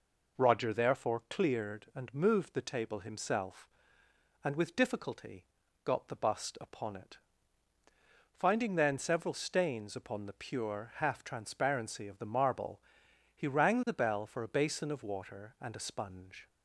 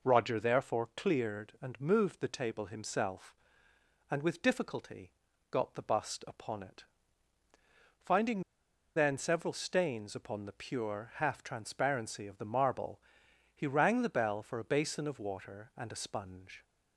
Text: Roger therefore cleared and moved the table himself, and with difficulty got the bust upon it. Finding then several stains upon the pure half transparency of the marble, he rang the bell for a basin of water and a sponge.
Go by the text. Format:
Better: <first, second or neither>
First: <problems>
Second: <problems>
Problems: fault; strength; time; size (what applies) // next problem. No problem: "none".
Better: first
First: pauses between "difficulty" and "got"; at 5.4 s; 0.38 s long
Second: pauses between "difficulty" and "got"; at 5.1 s; 0.38 s long // pauses between "Finding" and "then"; noticeable; at 8.4 s; 0.54 s long